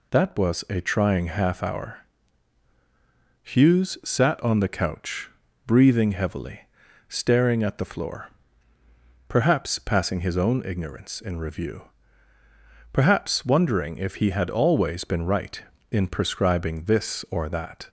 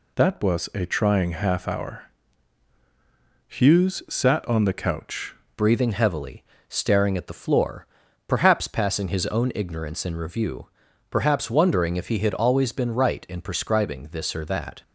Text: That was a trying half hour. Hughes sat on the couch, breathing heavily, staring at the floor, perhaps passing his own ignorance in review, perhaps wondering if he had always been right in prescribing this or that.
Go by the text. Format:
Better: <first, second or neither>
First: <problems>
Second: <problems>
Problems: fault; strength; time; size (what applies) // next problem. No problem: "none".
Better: first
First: none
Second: changes voice at "breathing"; from 5.5 s on; 9.3 s long